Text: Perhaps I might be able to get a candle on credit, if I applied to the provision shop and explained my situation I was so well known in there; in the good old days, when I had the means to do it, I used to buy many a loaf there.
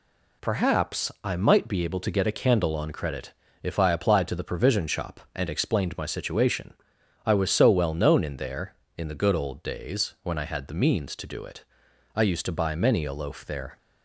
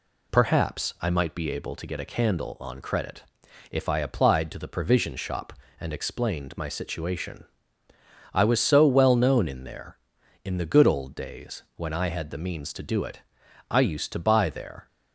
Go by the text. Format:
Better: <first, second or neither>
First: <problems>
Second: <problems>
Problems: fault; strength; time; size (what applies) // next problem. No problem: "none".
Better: first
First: pauses between "situation" and "I"; noticeable; at 6.7 s; 0.52 s long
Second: pauses between "situation" and "I"; noticeable; at 7.4 s; 0.88 s long // skips "many a loaf"; at 14.4 s